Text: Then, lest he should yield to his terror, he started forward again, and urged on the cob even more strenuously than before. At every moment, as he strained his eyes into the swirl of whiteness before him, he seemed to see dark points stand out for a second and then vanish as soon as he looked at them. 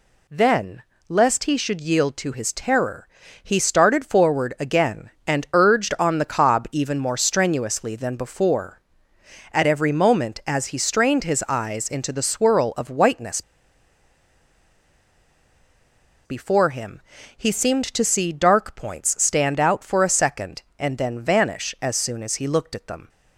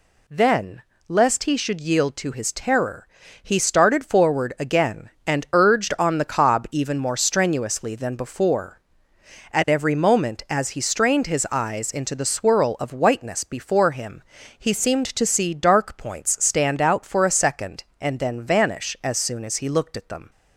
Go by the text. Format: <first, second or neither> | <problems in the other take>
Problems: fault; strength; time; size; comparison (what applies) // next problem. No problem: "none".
second | pauses between "whiteness" and "before"; strong; at 13.4 s; 2.8 s long